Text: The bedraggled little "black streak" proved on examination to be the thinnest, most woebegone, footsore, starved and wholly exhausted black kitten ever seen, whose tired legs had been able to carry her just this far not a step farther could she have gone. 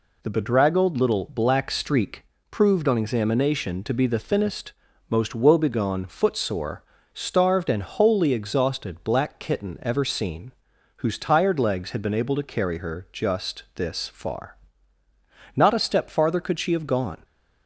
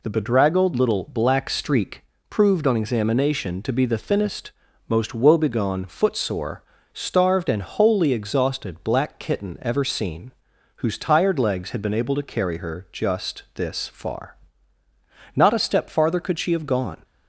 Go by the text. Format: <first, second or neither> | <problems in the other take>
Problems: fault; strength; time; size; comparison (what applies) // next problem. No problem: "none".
neither | pauses between "streak" and "proved"; slight; the same in both // pauses between "far" and "not"; the same in both